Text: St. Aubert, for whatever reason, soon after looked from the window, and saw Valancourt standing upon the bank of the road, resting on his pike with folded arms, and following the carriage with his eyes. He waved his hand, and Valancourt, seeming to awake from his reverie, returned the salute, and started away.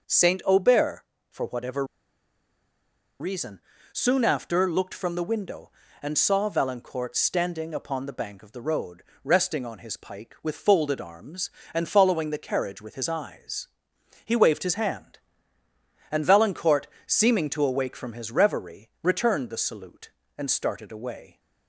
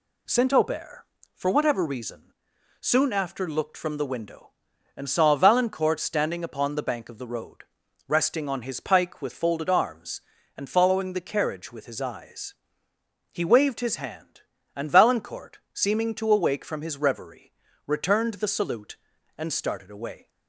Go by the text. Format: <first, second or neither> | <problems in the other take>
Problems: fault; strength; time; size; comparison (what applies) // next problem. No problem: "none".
second | starts louder than the rest; noticeable; until 1.3 s; 6 dB // pauses between "whatever" and "reason"; strong; at 1.8 s; 1.3 s long